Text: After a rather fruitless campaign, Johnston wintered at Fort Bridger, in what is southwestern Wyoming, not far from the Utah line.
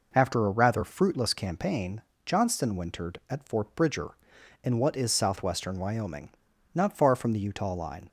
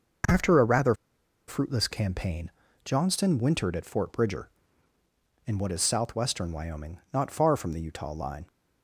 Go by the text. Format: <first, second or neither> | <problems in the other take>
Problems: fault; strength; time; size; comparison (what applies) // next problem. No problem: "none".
first | pauses between "rather" and "fruitless"; noticeable; at 0.9 s; 0.52 s long